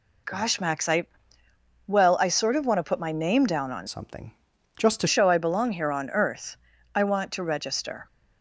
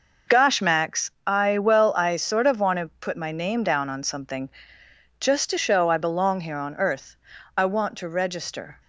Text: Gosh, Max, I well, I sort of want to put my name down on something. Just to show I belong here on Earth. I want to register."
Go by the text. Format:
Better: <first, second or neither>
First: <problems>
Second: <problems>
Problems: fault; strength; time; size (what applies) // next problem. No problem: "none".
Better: second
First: pauses between "I" and "well"; noticeable; at 1.0 s; 0.80 s long // changes voice from "something" to "to"; from 3.8 to 5.0 s; 1.2 s long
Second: none